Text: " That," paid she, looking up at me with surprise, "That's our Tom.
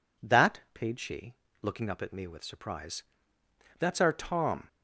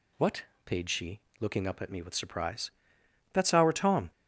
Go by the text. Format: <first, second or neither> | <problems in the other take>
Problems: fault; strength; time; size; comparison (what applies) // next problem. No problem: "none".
first | says "What" for "That"; at 0.1 s